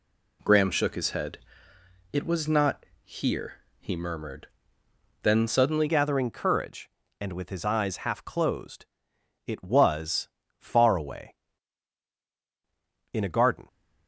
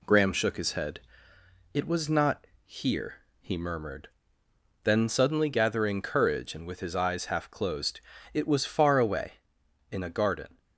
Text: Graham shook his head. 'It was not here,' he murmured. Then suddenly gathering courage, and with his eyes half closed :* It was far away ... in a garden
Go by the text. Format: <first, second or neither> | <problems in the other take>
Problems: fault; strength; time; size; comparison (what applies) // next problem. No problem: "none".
second | pauses between "not" and "here"; slight; at 2.8 s; 0.18 s long; slight in the second // changes voice at "gathering"; from 5.8 s on; 7.8 s long // pauses between "was" and "far"; slight; at 10.2 s; 0.28 s long